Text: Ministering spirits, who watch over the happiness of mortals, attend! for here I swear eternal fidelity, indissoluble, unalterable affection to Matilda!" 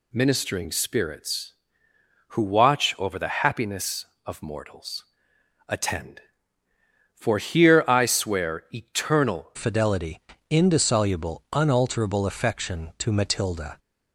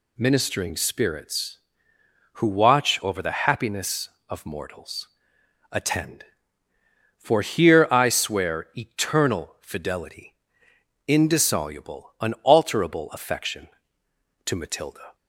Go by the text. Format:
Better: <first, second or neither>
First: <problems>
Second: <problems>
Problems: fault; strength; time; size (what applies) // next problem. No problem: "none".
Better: second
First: changes voice at "fidelity"; from 9.5 s on; 4.2 s long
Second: none